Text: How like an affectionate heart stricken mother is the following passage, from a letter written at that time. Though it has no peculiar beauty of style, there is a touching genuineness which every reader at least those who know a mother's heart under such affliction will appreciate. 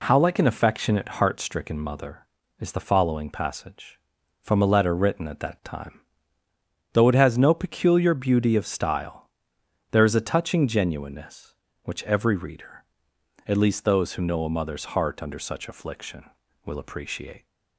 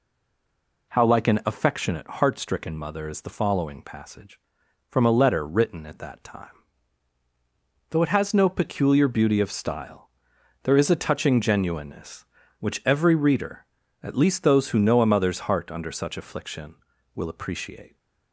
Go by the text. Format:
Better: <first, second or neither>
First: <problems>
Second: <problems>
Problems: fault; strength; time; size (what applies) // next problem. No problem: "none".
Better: first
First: none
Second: stays silent before the first word; slight; until 0.9 s; 0.9 s long